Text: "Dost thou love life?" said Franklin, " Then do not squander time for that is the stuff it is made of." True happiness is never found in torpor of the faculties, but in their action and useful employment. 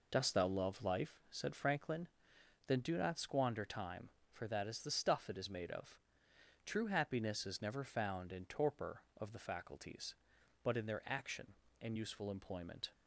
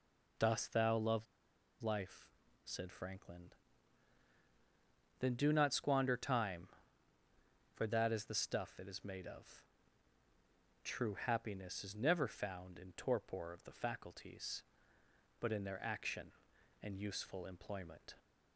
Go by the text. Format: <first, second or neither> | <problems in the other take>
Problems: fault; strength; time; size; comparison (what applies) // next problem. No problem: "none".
first | pauses between "love" and "life"; noticeable; at 1.2 s; 0.57 s long